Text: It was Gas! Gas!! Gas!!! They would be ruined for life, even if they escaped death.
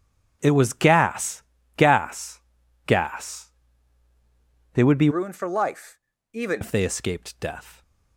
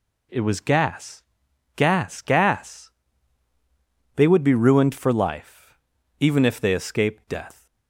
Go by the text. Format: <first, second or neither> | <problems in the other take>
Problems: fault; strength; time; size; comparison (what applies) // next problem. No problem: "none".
second | starts louder than the rest; strong; until 1.4 s; 8 dB // changes voice from "ruined" to "even"; from 5.0 to 6.6 s; 1.6 s long